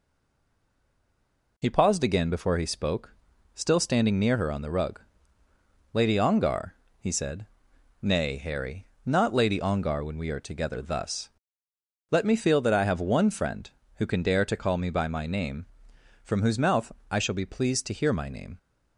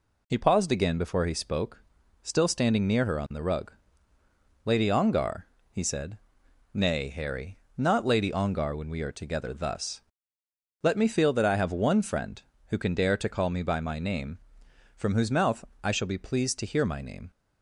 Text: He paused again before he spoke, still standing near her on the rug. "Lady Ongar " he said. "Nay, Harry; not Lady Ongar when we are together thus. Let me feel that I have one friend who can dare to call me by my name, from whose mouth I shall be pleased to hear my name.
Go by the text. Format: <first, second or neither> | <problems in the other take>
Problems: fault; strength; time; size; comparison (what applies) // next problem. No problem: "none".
second | stays silent before the first word; noticeable; until 1.5 s; 1.5 s long // pauses between "mouth" and "I"; slight; at 16.9 s; 0.18 s long; slight in the second